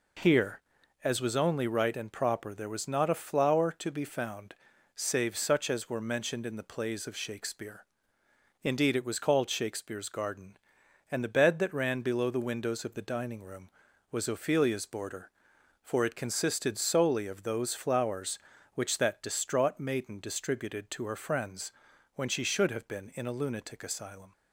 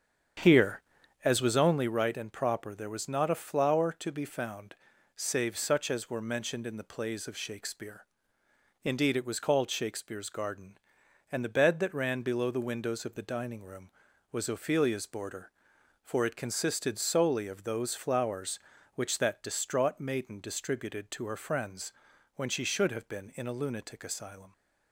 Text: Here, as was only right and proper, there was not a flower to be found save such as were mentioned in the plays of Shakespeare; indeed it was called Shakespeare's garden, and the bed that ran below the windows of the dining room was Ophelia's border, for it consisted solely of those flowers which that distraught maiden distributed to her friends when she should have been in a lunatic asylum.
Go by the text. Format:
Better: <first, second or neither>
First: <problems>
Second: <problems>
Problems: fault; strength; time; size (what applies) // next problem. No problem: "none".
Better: first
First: pauses between "found" and "save"; at 4.5 s; 0.40 s long // pauses between "friends" and "when"; at 21.7 s; 0.44 s long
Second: starts louder than the rest; strong; until 1.9 s; 8 dB // pauses between "found" and "save"; at 4.7 s; 0.40 s long // pauses between "friends" and "when"; at 21.9 s; 0.44 s long